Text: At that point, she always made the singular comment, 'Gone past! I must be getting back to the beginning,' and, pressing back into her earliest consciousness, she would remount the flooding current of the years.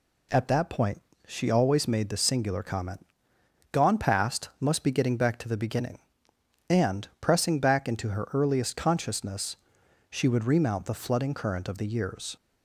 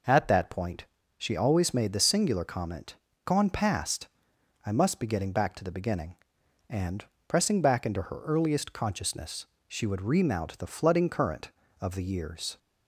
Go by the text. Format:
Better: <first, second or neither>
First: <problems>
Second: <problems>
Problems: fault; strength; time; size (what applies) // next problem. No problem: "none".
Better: second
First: skips "I"; at 4.5 s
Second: none